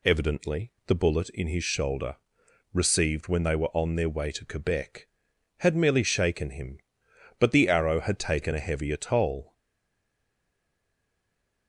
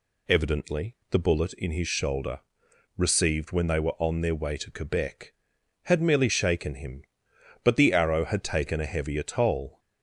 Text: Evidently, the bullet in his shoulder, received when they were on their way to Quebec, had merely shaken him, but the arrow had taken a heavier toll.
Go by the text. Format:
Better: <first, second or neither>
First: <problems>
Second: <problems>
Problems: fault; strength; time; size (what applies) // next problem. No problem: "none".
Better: second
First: stays silent after the last word; from 9.5 s on; 2.1 s long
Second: none